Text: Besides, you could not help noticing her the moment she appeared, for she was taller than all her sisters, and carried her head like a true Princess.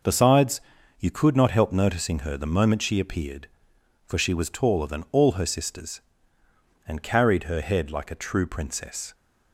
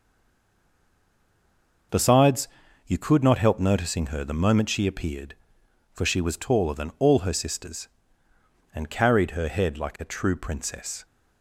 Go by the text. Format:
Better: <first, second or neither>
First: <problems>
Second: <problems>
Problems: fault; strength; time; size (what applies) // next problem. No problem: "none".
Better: first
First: none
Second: stays silent before the first word; noticeable; until 1.9 s; 1.9 s long